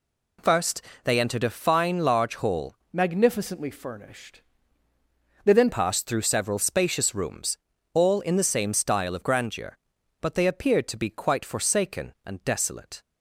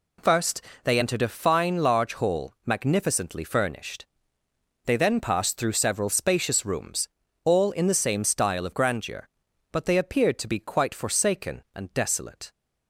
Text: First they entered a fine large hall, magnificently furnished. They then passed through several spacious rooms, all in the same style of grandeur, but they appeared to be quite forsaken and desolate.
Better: second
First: pauses between "First" and "they"; slight; at 0.8 s; 0.22 s long // changes voice from "magnificently" to "then"; from 2.9 to 5.6 s; 2.7 s long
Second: pauses between "First" and "they"; slight; at 0.6 s; 0.22 s long

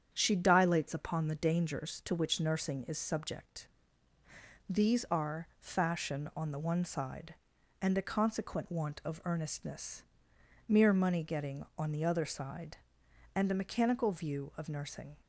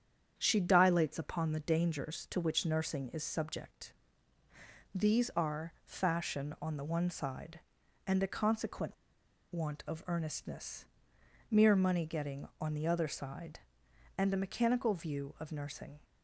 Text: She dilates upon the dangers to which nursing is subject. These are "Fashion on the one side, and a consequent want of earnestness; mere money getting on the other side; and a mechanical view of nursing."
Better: first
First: starts louder than the rest; strong; until 1.1 s; 8.5 dB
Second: starts louder than the rest; strong; until 1.3 s; 8.5 dB // pauses between "consequent" and "want"; noticeable; at 8.9 s; 0.58 s long

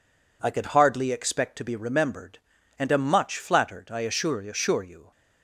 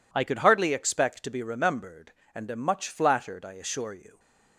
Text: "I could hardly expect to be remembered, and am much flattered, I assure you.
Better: second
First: says "assure" twice; at 4.4 s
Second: none

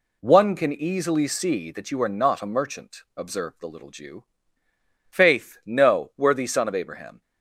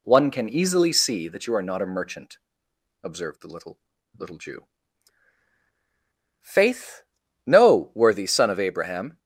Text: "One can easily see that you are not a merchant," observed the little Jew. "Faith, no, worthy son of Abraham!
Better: first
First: none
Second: says "little" twice; at 4.1 s

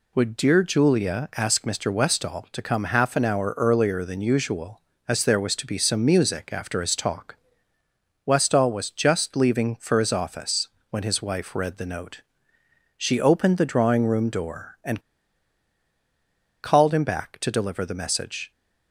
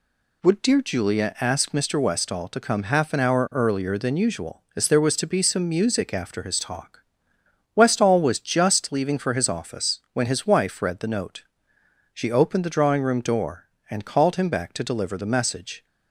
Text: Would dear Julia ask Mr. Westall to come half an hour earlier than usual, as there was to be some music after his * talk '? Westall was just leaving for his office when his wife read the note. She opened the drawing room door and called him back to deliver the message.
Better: second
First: pauses between "office" and "when"; slight; at 10.6 s; 0.22 s long // pauses between "and" and "called"; strong; at 14.9 s; 1.6 s long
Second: none

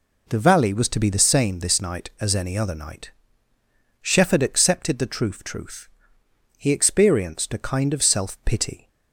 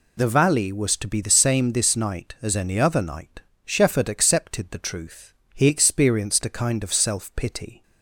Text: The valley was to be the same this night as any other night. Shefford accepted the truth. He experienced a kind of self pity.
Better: second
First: says "truth" twice; at 5.4 s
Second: none

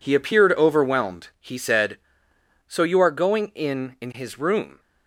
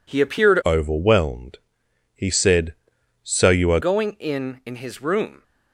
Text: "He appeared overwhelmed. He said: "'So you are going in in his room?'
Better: first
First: none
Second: changes voice from "overwhelmed" to "are"; from 0.6 to 3.7 s; 3.1 s long

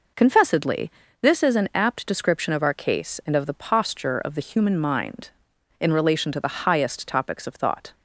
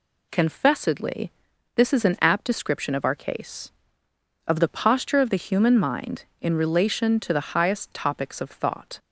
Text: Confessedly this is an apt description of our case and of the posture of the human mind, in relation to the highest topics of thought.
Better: first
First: pauses between "Confessedly" and "this"; slight; at 0.9 s; 0.32 s long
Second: pauses between "Confessedly" and "this"; at 1.3 s; 0.44 s long // skips "and"; at 4.0 s

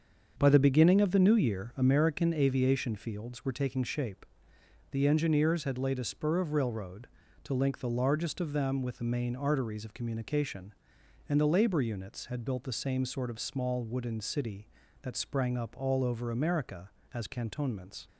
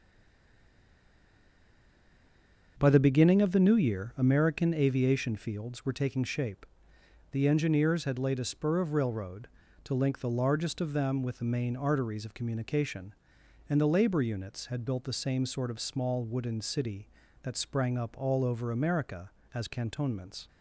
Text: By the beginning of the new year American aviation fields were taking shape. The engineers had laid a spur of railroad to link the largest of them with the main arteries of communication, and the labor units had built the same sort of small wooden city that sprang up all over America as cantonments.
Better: first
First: starts louder than the rest; until 1.3 s; 7 dB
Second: stays silent before the first word; strong; until 2.7 s; 2.7 s long // starts louder than the rest; until 3.8 s; 7 dB

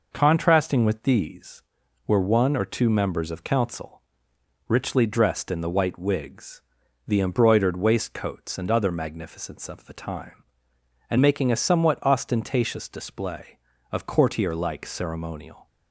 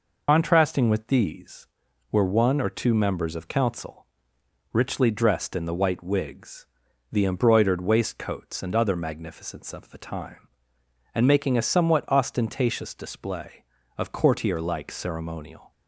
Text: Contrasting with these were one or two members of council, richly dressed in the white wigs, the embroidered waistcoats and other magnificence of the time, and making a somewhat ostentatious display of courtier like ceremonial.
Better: first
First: none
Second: loses the start of "Contrasting"; at 0.2 s; 105 ms

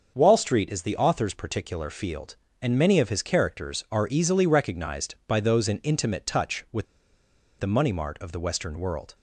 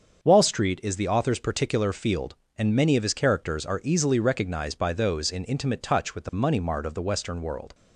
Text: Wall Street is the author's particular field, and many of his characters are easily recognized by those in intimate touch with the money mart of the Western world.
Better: second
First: starts louder than the rest; until 1.1 s; 6.5 dB // pauses between "with" and "the"; noticeable; at 6.8 s; 0.75 s long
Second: starts louder than the rest; until 1.2 s; 6.5 dB

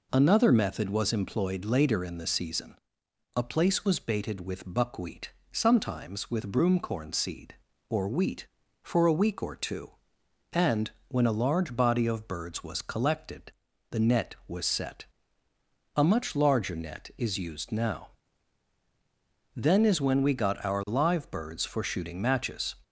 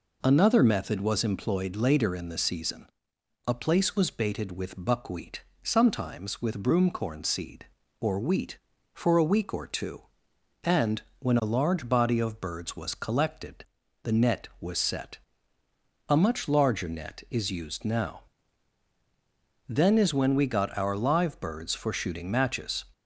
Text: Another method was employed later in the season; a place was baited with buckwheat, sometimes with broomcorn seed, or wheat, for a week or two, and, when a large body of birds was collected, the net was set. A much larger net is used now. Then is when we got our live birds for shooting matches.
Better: neither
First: none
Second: none

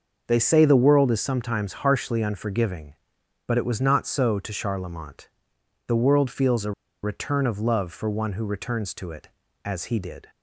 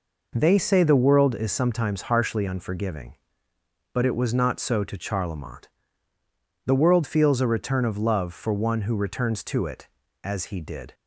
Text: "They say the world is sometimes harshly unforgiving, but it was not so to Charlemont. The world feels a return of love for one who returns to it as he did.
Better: second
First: starts louder than the rest; noticeable; until 1.2 s; 6 dB // pauses between "a" and "return"; slight; at 6.7 s; 0.31 s long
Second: none

